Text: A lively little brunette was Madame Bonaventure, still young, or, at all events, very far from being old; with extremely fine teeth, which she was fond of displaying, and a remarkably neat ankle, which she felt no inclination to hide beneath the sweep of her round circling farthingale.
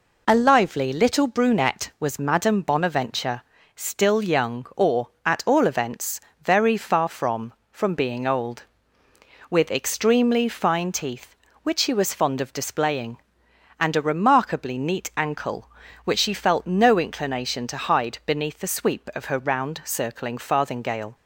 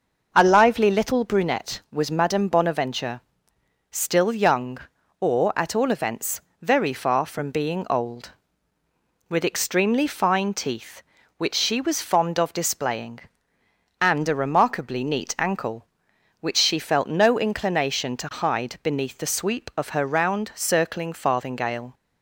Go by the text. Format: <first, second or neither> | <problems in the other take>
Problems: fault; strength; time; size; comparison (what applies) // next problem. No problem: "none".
second | says "from" twice; at 7.7 s